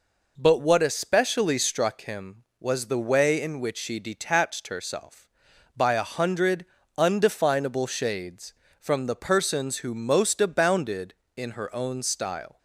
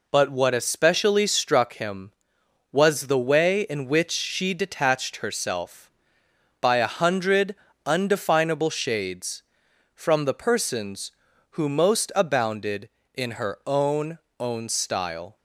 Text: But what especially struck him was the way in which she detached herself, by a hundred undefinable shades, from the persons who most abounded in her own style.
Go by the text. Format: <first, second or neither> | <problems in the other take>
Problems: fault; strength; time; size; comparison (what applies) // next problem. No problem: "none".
first | pauses between "hundred" and "undefinable"; slight; at 7.5 s; 0.30 s long; slight in the first // says "own" twice; at 14.3 s